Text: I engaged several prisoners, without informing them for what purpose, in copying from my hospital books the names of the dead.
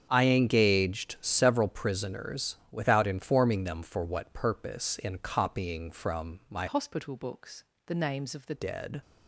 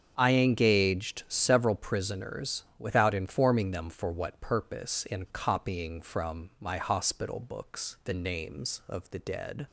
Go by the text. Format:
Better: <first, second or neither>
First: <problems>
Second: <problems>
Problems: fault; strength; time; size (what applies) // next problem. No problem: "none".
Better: second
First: starts louder than the rest; strong; until 1.1 s; 7.5 dB // changes voice from "hospital" to "the"; from 6.6 to 8.5 s; 1.9 s long // pauses between "books" and "the"; slight; at 7.6 s; 0.20 s long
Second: starts louder than the rest; strong; until 1.1 s; 7 dB